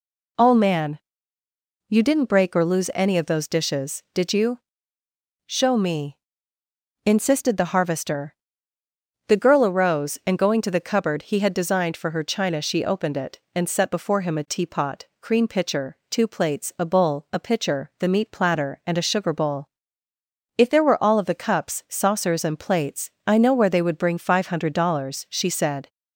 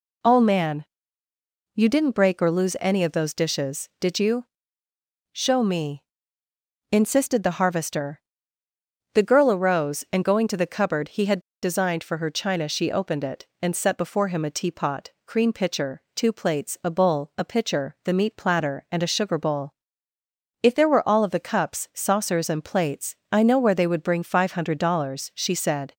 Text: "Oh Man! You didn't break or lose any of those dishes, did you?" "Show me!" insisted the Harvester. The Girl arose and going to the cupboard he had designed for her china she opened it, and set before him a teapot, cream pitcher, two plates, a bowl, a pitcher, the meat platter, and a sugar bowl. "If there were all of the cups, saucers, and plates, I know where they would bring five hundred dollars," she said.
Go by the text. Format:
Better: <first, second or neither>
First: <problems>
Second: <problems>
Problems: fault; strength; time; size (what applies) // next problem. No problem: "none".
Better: first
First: none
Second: pauses between "had" and "designed"; slight; at 11.3 s; 0.23 s long